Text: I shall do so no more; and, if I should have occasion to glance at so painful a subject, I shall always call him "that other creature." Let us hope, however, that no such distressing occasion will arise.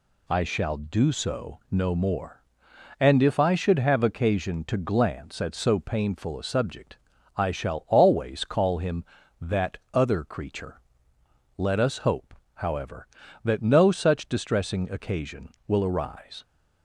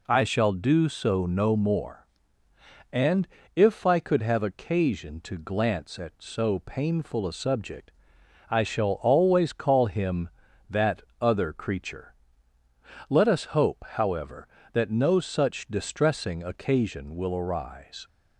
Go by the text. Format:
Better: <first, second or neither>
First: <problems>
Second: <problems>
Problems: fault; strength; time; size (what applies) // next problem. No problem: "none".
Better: first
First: pauses between "that" and "other"; slight; at 9.7 s; 0.16 s long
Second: says "could" for "should"; at 3.9 s // pauses between "that" and "other"; slight; at 11.0 s; 0.18 s long